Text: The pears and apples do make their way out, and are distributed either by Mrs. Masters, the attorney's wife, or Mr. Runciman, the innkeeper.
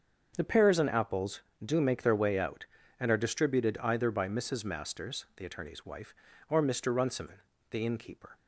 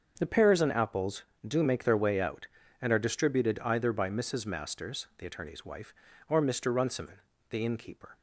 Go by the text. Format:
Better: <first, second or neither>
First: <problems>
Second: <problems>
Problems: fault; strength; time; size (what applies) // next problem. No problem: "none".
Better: neither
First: starts louder than the rest; until 1.3 s; 7 dB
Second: starts louder than the rest; until 1.1 s; 7 dB